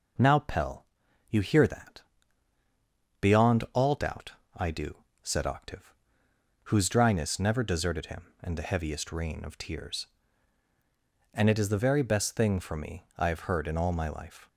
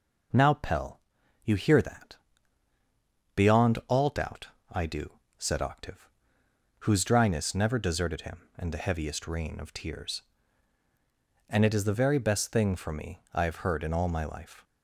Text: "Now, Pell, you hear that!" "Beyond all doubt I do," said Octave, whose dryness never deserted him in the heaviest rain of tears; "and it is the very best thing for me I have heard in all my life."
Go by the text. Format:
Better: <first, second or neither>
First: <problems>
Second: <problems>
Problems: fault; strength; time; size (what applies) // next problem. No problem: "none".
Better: neither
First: pauses between "doubt" and "I"; slight; at 4.3 s; 0.24 s long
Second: pauses between "doubt" and "I"; slight; at 4.4 s; 0.24 s long